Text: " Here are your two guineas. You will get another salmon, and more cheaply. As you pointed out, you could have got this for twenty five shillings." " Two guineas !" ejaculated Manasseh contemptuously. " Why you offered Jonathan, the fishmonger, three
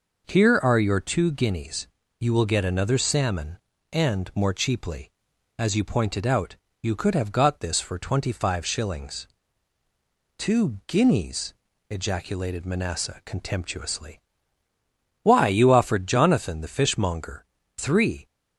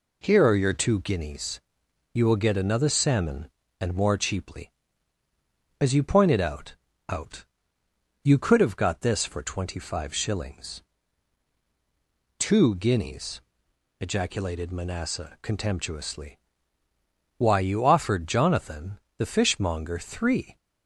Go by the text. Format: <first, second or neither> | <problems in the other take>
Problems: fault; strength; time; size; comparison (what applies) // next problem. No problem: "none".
first | says "out" twice; at 7.0 s